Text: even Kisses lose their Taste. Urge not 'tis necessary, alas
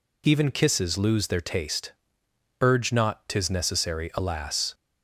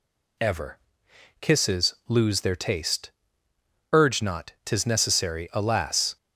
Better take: first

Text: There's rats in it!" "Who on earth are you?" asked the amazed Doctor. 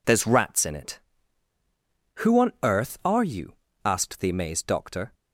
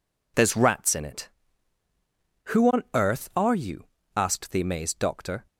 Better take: neither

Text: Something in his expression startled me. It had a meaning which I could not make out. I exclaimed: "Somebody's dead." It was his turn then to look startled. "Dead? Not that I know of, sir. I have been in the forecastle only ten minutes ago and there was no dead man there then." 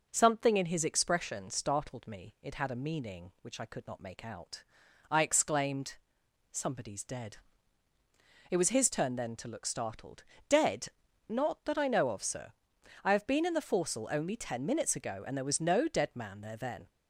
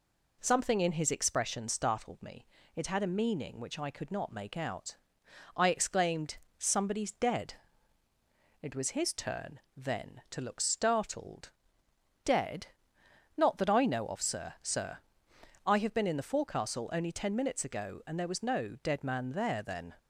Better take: first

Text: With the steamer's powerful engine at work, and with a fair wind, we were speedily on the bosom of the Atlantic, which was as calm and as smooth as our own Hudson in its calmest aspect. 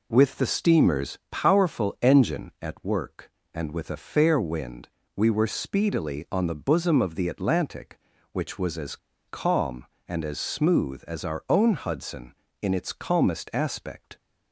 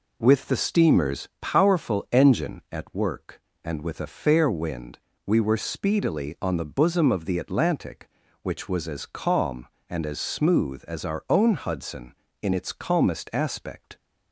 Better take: second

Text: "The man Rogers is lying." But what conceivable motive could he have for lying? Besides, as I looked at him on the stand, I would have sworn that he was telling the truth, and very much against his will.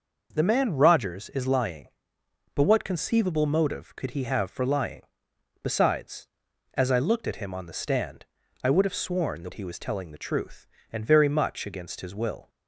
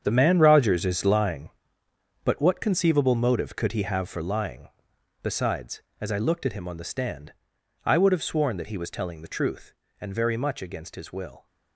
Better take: first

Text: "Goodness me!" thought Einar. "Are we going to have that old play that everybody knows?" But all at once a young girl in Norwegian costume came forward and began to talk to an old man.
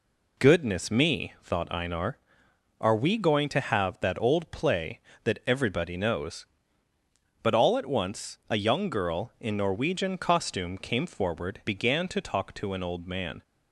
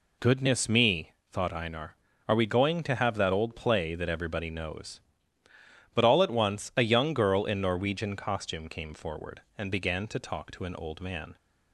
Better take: second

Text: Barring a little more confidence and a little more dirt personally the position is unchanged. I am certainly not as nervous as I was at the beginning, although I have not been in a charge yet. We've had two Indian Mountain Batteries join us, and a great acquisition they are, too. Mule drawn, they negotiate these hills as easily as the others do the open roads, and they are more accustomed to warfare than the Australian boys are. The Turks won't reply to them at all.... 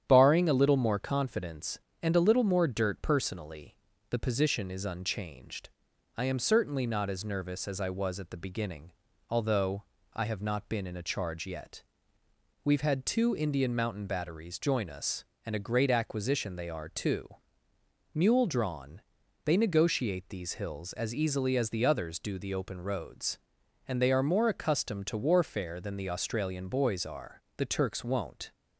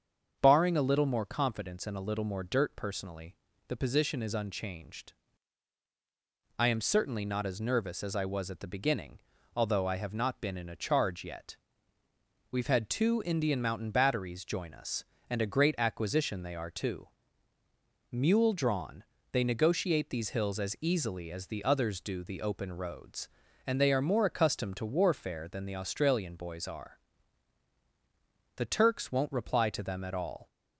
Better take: second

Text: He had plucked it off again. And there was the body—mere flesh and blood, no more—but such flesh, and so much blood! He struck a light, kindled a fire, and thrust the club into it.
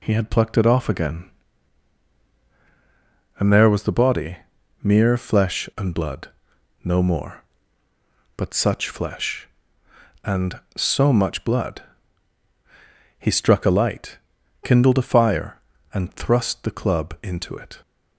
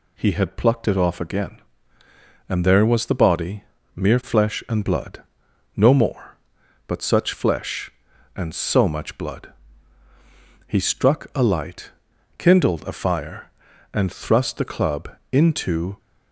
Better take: first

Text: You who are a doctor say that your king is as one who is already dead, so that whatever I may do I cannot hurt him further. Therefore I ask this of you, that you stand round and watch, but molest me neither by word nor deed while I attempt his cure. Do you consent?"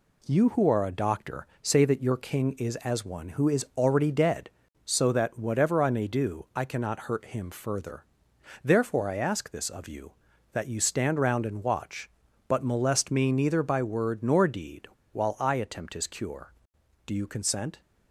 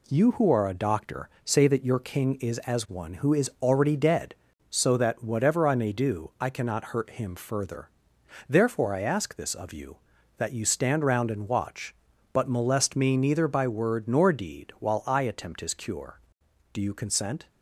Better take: second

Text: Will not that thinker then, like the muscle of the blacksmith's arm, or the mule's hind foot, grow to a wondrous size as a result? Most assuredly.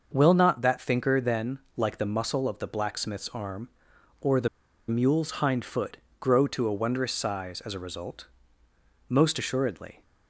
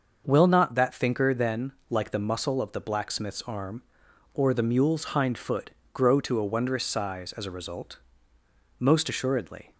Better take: second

